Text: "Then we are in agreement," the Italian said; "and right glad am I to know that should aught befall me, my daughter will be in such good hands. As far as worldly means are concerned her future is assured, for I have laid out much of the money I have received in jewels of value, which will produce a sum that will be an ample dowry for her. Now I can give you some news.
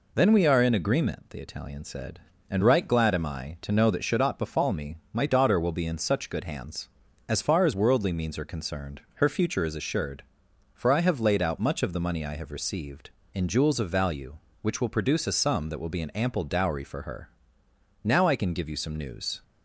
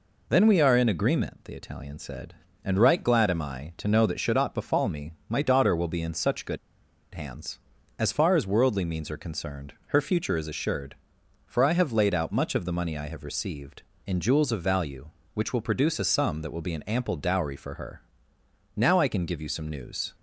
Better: first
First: none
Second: pauses between "good" and "hands"; noticeable; at 6.5 s; 0.57 s long

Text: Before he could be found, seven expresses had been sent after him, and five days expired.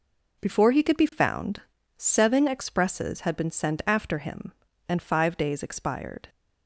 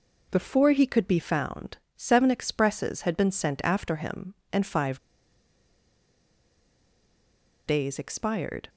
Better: first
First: none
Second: pauses between "five" and "days"; strong; at 4.9 s; 2.6 s long

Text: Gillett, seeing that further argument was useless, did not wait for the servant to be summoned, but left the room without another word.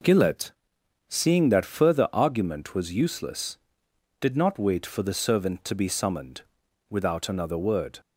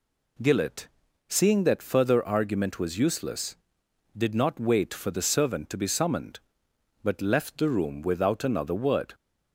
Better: second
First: skips "but left the room"; at 6.6 s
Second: none

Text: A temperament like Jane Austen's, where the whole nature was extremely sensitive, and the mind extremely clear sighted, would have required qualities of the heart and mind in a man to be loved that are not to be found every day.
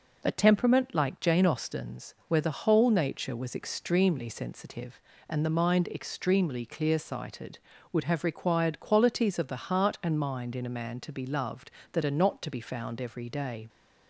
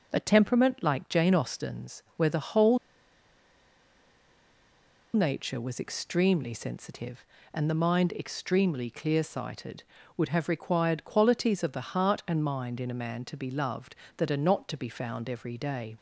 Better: first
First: none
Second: pauses between "whole" and "nature"; strong; at 2.7 s; 2.3 s long

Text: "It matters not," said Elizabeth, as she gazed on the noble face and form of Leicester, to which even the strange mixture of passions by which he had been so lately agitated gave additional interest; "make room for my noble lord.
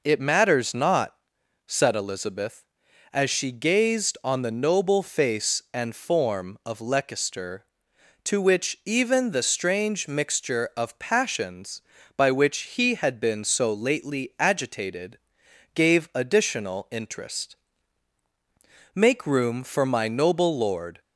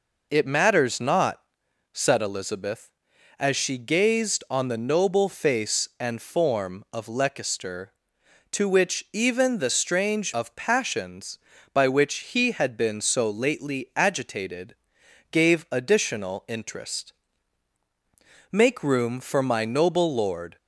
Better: first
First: pauses between "agitated" and "gave"; noticeable; at 15.1 s; 0.56 s long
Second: skips "mixture"; at 10.3 s // pauses between "agitated" and "gave"; noticeable; at 14.7 s; 0.56 s long

